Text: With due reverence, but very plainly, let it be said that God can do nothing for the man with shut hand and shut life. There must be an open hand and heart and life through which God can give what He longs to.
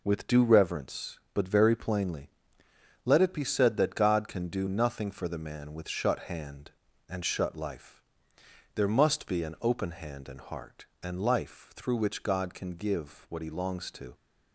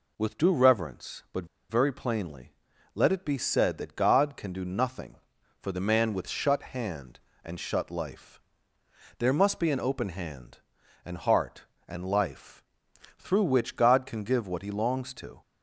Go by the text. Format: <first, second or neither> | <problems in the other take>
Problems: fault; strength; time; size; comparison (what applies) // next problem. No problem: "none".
first | pauses between "but" and "very"; slight; at 1.4 s; 0.23 s long // pauses between "life" and "through"; noticeable; at 12.6 s; 0.54 s long